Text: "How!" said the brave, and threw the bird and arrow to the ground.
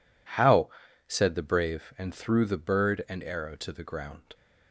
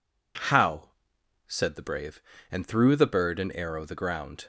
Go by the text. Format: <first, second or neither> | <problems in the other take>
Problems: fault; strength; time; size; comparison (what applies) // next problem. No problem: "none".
first | skips "to"; at 3.8 s